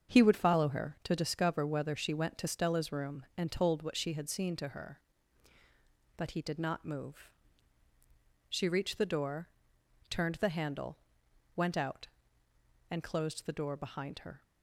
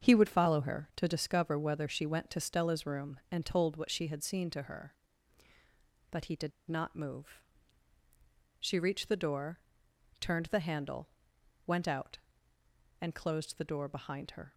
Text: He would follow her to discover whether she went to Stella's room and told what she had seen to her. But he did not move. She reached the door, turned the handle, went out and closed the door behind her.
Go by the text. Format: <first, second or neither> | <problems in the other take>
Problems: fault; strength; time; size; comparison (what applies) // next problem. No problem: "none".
first | starts louder than the rest; until 1.1 s; 7 dB; also in the first // pauses between "did" and "not"; slight; at 6.5 s; 0.17 s long